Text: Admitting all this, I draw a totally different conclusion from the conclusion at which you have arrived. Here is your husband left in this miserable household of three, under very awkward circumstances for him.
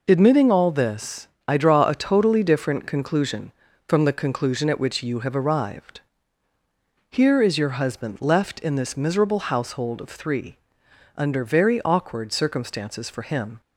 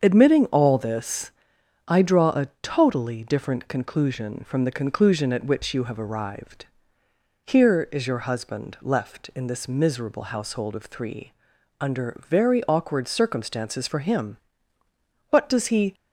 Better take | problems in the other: first | starts louder than the rest; until 1.0 s; 7 dB // goes on to say "What does he"; noticeable; from 15.2 s on; 0.64 s long

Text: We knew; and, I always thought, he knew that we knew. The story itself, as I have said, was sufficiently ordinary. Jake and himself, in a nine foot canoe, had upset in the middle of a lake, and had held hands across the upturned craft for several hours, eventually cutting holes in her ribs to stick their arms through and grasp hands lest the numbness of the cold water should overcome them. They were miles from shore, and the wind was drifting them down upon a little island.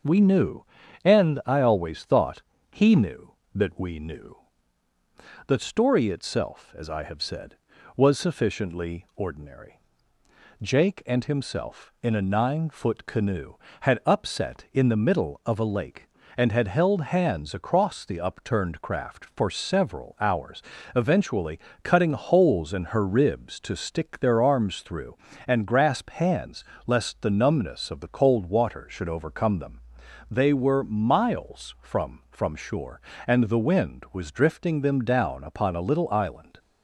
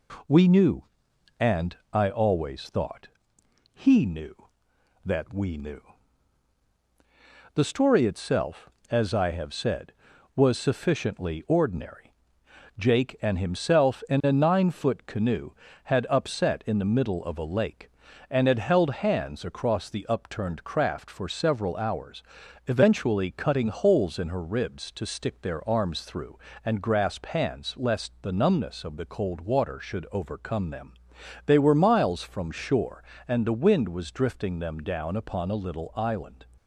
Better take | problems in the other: second | starts louder than the rest; noticeable; until 1.4 s; 6 dB // pauses between "eventually" and "cutting"; slight; at 21.6 s; 0.24 s long // pauses between "hands" and "lest"; slight; at 26.6 s; 0.22 s long // says "from" twice; at 32.3 s

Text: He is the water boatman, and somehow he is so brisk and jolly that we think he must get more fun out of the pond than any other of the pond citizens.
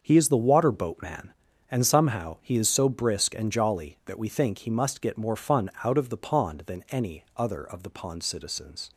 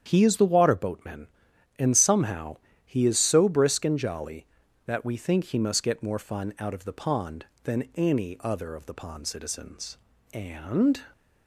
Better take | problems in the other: first | starts louder than the rest; strong; until 1.0 s; 8.5 dB; also in the first // pauses between "somehow" and "he"; slight; at 2.5 s; 0.26 s long // goes on to say "And"; noticeable; from 10.3 s on; 0.68 s long

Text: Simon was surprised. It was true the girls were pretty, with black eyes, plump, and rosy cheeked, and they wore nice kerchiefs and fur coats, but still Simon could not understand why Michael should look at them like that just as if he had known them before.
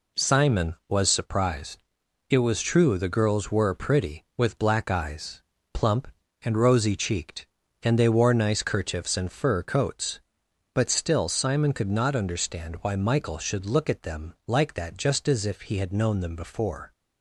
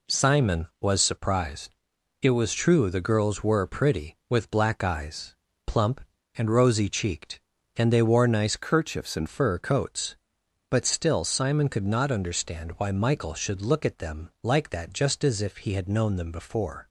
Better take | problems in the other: first | changes voice from "kerchiefs" to "and"; from 8.5 to 9.2 s; 0.7 s long

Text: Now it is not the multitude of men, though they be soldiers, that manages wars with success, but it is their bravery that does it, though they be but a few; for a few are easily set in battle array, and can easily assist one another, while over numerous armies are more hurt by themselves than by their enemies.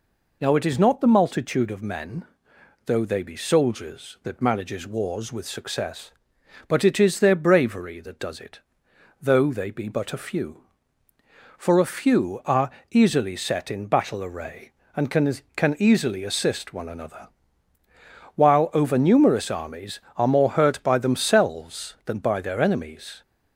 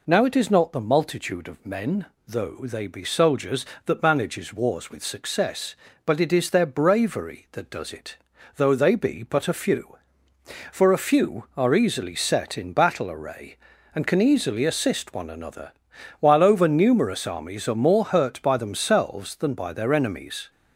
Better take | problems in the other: second | pauses between "are" and "easily"; slight; at 12.6 s; 0.20 s long // says "can" twice; at 15.5 s

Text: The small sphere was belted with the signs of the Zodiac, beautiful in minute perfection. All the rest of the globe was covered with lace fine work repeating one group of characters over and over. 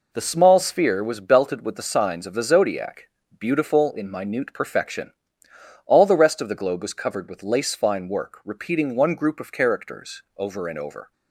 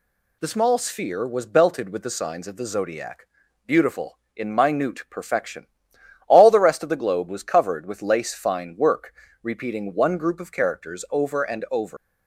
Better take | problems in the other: first | pauses between "work" and "repeating"; slight; at 9.1 s; 0.28 s long // leaves "over" unfinished; at 11.9 s; 95 ms

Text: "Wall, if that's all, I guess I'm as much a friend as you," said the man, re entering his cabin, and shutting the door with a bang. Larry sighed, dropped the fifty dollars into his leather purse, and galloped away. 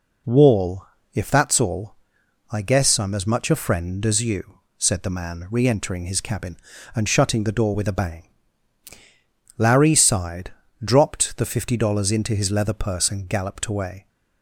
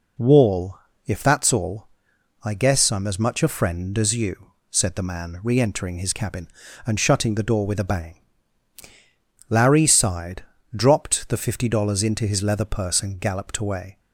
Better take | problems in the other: neither | none

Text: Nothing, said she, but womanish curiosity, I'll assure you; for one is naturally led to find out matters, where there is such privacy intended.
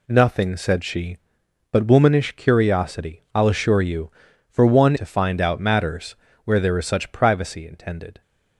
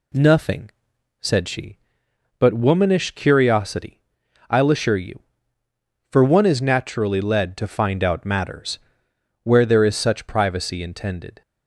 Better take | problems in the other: second | skips "is naturally led"; at 4.9 s

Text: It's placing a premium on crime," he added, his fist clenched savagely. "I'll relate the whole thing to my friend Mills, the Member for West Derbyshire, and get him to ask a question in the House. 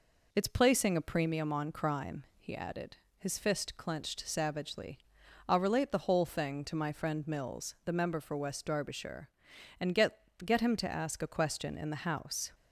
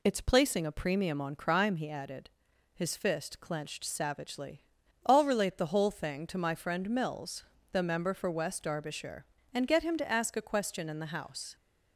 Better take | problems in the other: second | says "get" twice; at 10.4 s

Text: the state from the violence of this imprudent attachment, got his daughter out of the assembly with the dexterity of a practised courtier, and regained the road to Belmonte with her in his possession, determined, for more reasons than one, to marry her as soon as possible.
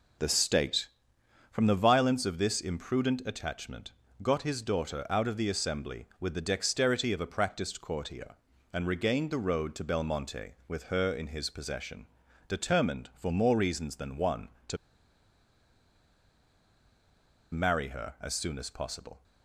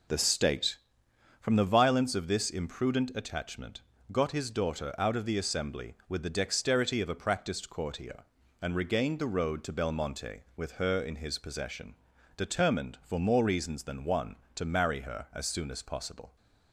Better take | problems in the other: second | pauses between "to" and "marry"; strong; at 14.7 s; 2.7 s long

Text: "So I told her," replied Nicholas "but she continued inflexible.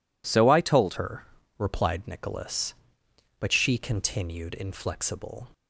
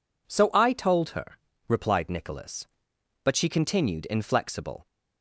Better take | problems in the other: second | changes voice at "her"; from 0.9 s on; 4.5 s long

